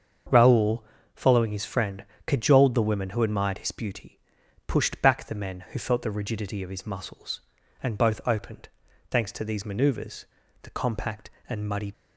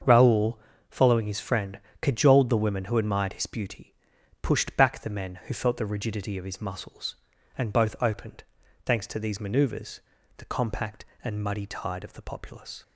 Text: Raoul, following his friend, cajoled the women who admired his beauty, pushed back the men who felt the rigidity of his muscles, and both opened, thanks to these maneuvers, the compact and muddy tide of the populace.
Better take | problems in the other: second | starts louder than the rest; until 1.6 s; 7 dB; also in the second // stops before "tide of the populace"; at 11.9 s

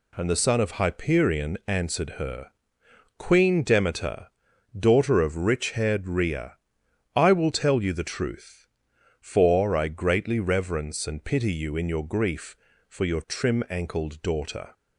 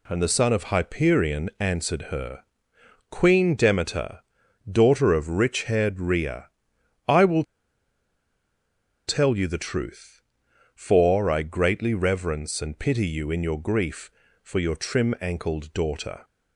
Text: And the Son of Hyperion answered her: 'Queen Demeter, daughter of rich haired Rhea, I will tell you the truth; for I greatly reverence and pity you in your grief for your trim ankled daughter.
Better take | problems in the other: first | pauses between "will" and "tell"; strong; at 7.4 s; 1.6 s long

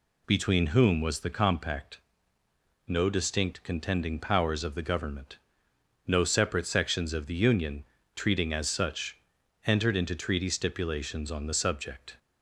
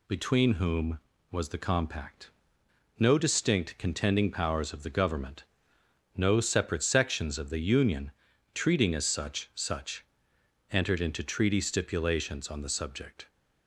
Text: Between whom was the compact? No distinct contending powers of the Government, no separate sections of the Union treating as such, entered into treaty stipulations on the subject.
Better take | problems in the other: first | pauses between "Union" and "treating"; at 8.1 s; 0.44 s long; slight in the first // says "such" twice; at 9.5 s

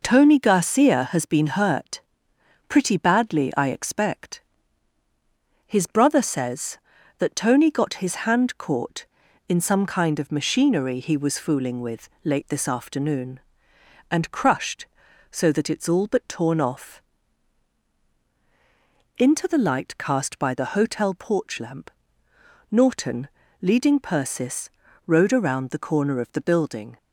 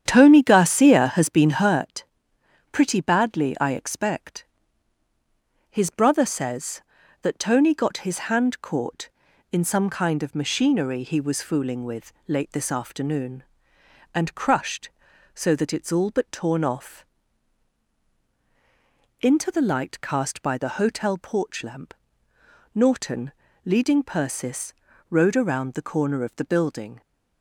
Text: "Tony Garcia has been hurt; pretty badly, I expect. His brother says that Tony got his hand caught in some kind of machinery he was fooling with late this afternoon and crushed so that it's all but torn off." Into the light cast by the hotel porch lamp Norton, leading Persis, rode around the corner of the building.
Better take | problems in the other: first | starts louder than the rest; strong; until 1.9 s; 9 dB // pauses between "with" and "late"; slight; at 12.1 s; 0.16 s long; slight in the first // pauses between "lamp" and "Norton"; noticeable; at 21.9 s; 0.80 s long; noticeable in the first

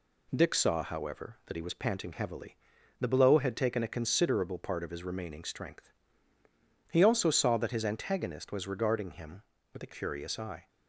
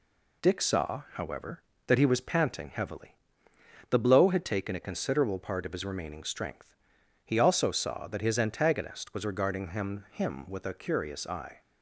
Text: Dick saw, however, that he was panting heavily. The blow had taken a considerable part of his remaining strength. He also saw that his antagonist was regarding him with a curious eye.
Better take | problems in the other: first | says "him" twice; at 10.1 s

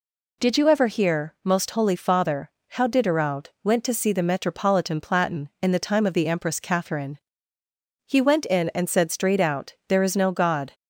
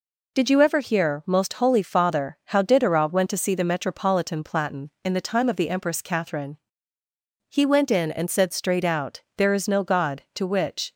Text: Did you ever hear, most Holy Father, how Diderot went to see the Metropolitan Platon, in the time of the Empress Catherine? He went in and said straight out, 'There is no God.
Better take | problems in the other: first | goes on to say "To which"; from 10.3 s on; 0.58 s long

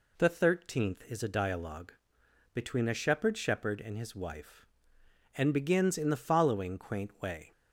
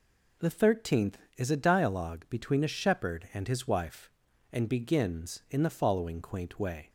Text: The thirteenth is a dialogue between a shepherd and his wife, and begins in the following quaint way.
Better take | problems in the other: second | pauses between "dialogue" and "between"; noticeable; at 1.9 s; 0.62 s long // says "shepherd" twice; at 3.3 s

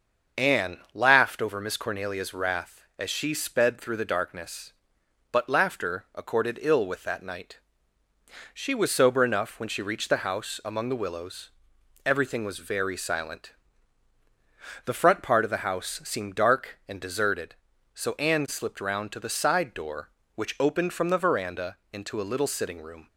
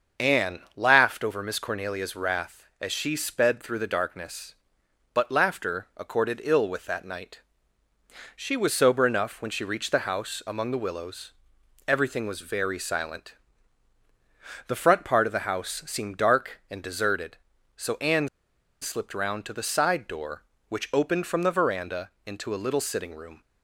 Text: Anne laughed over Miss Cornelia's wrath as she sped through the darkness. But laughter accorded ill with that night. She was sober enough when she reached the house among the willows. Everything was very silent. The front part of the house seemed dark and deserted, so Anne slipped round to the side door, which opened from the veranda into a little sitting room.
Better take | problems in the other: first | starts louder than the rest; until 1.3 s; 6.5 dB; also in the first // pauses between "Anne" and "laughed"; slight; at 0.5 s; 0.16 s long; slight in the first // pauses between "Anne" and "slipped"; noticeable; at 18.2 s; 0.53 s long // pauses between "veranda" and "into"; slight; at 22.0 s; 0.16 s long; slight in the first

